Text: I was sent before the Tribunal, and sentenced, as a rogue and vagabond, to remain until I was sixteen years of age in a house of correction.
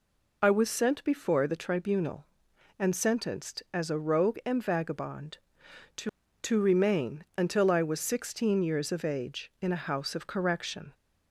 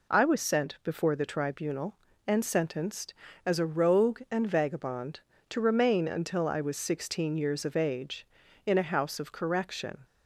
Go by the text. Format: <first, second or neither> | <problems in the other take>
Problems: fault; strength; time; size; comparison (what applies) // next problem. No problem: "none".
second | says "to" twice; at 6.4 s